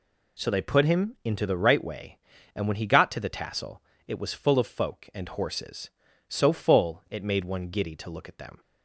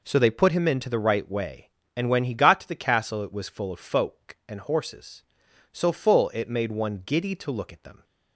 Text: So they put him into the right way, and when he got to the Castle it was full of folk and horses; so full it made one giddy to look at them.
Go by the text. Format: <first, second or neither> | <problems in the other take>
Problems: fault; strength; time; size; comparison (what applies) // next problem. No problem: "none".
second | says "Tassel" for "Castle"; at 3.2 s